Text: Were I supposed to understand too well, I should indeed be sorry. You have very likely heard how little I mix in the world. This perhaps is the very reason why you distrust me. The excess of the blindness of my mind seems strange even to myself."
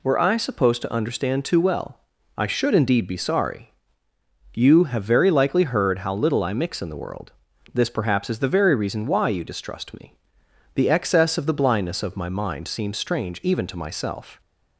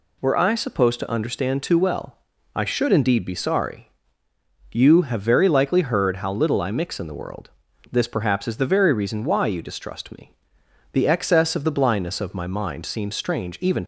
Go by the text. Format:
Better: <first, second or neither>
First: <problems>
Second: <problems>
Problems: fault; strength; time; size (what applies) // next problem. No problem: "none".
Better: first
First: none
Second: stops before "to myself"; at 13.8 s